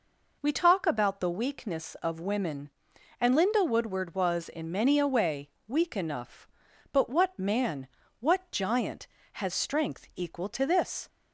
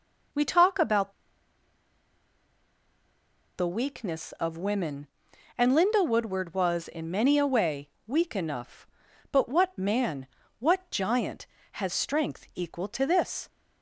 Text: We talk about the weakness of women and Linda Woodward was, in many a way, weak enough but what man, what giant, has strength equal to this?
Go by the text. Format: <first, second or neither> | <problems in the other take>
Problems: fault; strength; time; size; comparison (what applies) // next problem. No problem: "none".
first | pauses between "about" and "the"; strong; at 1.1 s; 2.4 s long